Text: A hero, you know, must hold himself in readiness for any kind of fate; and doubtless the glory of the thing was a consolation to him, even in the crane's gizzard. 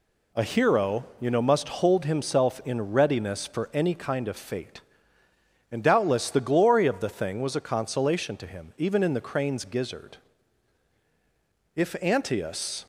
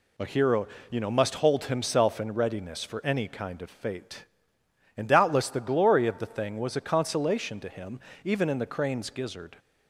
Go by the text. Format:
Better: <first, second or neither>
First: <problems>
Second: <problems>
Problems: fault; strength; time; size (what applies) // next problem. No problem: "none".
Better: second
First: goes on to say "If Antaeus"; noticeable; from 11.7 s on; 1.0 s long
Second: none